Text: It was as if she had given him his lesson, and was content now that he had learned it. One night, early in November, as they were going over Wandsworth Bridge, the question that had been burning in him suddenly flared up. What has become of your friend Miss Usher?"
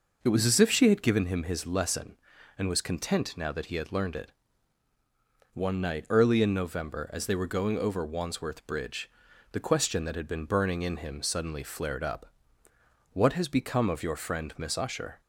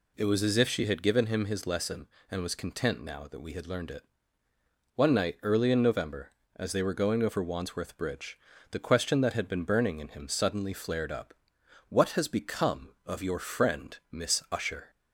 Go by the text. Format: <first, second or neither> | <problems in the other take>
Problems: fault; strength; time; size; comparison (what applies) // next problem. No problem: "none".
first | says "we" for "he"; at 3.4 s